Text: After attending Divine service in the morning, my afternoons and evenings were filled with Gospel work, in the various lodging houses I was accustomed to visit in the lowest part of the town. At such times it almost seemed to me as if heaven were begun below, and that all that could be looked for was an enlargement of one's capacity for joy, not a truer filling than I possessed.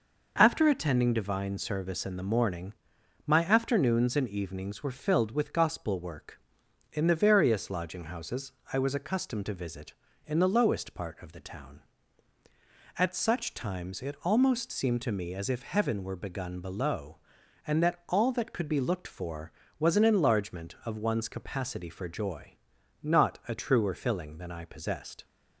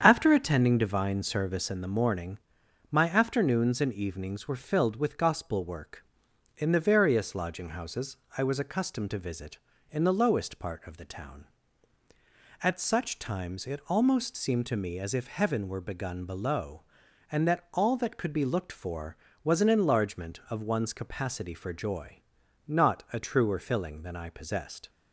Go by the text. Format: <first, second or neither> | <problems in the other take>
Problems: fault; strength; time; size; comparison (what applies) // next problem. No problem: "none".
first | starts louder than the rest; strong; until 1.8 s; 8 dB // pauses between "houses" and "I"; slight; at 8.1 s; 0.20 s long; slight in the first